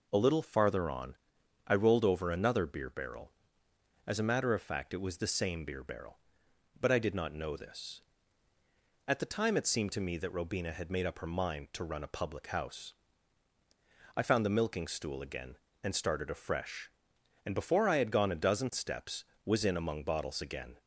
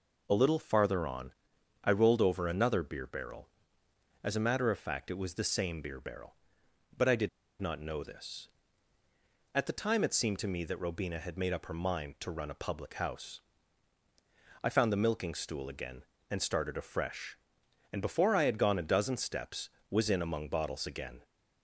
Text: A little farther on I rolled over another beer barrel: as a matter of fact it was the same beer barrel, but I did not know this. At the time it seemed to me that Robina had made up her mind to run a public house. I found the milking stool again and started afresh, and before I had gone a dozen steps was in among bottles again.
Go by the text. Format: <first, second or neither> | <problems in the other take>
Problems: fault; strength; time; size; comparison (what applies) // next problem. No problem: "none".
first | pauses between "on" and "I"; noticeable; at 1.3 s; 0.52 s long; noticeable in the first // pauses between "did" and "not"; slight; at 7.2 s; 0.31 s long